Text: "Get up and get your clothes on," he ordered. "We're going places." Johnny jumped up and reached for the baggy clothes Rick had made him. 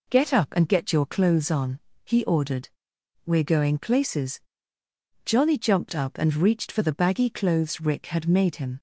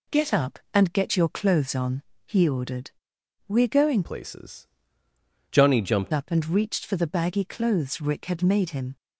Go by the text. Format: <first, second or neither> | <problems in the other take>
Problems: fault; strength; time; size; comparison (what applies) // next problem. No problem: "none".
first | changes voice from "places" to "jumped"; from 4.0 to 6.1 s; 2.1 s long